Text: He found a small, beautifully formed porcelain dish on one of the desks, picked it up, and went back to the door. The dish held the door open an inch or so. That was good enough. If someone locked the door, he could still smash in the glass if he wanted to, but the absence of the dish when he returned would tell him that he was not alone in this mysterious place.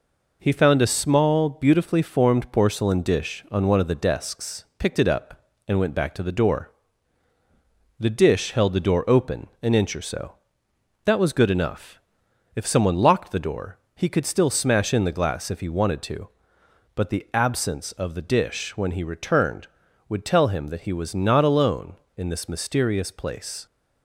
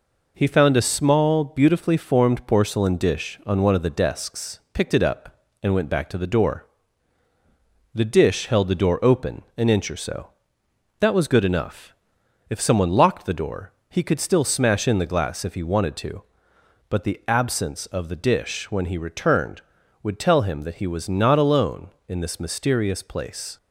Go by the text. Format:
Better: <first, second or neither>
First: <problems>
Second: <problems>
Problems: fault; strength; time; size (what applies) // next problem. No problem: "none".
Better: neither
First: none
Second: none